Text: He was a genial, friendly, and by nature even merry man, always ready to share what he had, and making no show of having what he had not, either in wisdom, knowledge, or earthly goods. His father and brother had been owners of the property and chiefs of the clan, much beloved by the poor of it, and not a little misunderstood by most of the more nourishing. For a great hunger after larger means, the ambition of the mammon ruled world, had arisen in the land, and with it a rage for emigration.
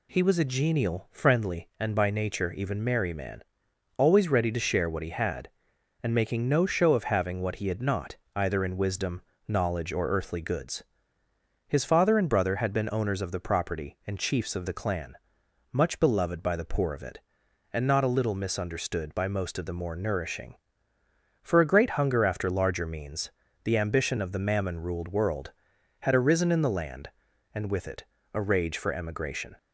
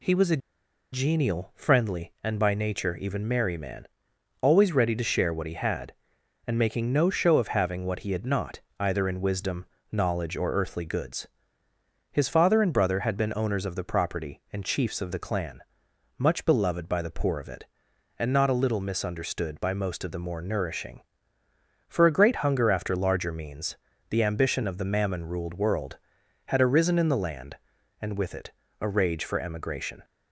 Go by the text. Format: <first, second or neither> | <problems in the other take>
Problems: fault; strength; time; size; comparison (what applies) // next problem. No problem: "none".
first | pauses between "a" and "genial"; noticeable; at 0.4 s; 0.53 s long // pauses between "it" and "a"; slight; at 28.5 s; 0.28 s long; slight in the first